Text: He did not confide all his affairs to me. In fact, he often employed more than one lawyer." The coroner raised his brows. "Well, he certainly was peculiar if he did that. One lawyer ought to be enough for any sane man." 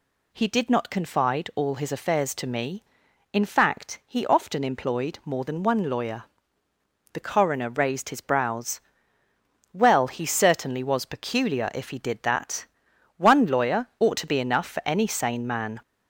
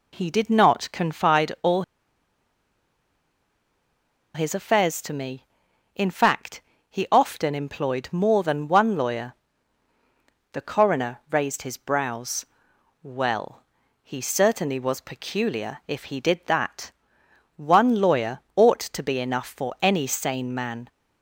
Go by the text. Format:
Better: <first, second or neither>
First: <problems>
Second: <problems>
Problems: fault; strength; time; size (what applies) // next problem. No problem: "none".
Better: first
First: none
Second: pauses between "all" and "his"; strong; at 1.8 s; 2.5 s long // pauses between "lawyer" and "ought"; slight; at 18.3 s; 0.16 s long